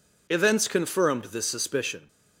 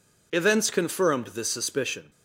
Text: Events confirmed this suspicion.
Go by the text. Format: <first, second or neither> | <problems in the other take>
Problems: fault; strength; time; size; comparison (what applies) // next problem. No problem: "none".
neither | none